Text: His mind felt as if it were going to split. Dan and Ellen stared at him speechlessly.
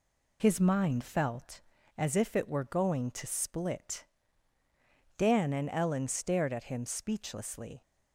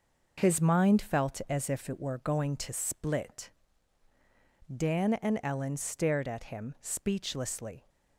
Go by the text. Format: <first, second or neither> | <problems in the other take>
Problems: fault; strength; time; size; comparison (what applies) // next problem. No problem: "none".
second | loses the start of "His"; at 0.3 s; 35 ms